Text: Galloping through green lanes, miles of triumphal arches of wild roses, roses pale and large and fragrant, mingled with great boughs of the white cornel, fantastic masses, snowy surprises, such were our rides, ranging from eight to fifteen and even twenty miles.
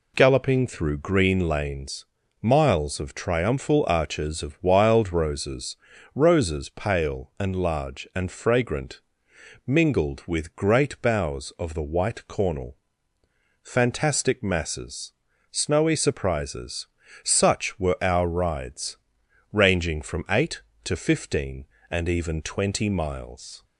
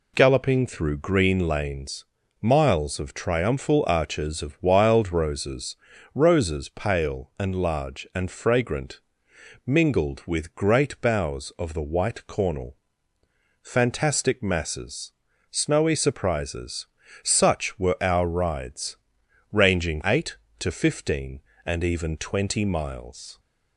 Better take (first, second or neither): first